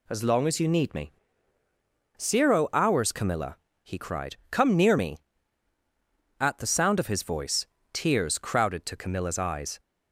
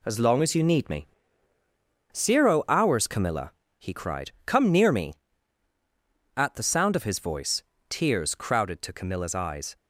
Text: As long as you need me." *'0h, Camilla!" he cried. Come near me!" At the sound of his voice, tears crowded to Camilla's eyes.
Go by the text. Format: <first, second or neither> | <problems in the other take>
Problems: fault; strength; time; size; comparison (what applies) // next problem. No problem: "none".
first | gets quieter; noticeable; throughout; 6 dB